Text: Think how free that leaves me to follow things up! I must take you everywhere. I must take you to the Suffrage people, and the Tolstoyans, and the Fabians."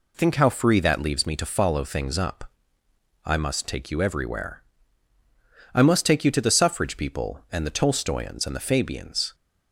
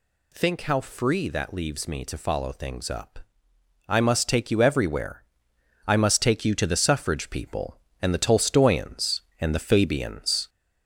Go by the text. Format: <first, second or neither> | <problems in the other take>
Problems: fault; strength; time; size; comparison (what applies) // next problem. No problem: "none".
first | gets louder; slight; throughout; 3 dB